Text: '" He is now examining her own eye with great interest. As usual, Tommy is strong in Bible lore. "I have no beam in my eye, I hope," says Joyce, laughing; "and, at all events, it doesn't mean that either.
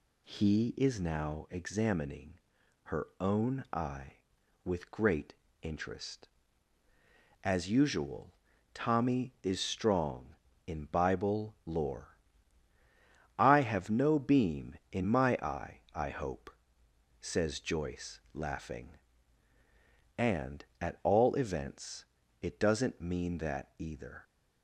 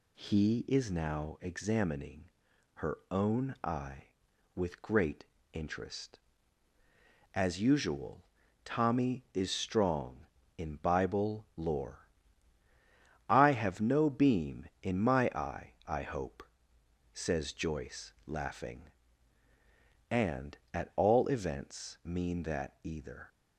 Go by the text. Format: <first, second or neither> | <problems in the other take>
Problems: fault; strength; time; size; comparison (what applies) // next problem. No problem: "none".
first | pauses between "examining" and "her"; noticeable; at 2.2 s; 0.46 s long; noticeable in the first // pauses between "great" and "interest"; slight; at 5.2 s; 0.26 s long; slight in the first // skips "it doesn't"; at 22.0 s